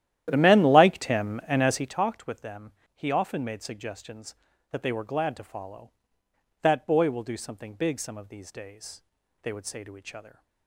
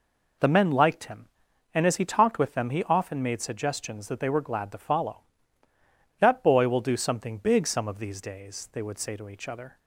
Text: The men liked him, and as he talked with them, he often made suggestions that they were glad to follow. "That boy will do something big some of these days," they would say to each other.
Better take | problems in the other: second | starts louder than the rest; strong; until 2.0 s; 12 dB

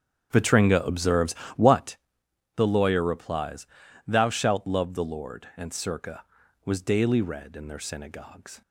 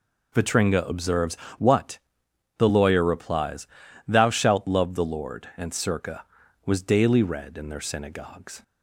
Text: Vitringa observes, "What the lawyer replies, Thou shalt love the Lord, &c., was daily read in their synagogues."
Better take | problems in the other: second | starts louder than the rest; strong; until 2.1 s; 9 dB // pauses between "What" and "the"; noticeable; at 1.9 s; 0.60 s long; noticeable in the second

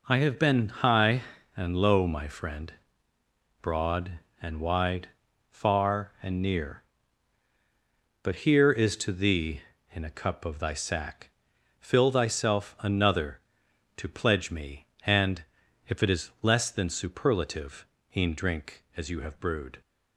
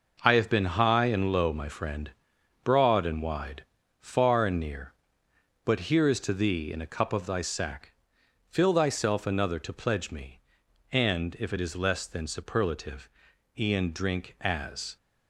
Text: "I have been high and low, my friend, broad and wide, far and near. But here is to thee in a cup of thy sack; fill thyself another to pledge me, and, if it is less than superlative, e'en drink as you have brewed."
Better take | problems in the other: first | stops before "you have brewed"; at 14.9 s

